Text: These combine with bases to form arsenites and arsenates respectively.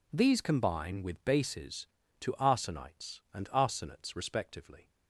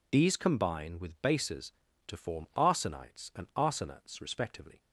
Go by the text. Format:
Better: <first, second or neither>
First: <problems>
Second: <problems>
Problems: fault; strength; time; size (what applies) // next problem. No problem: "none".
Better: second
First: skips "form"; at 2.3 s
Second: none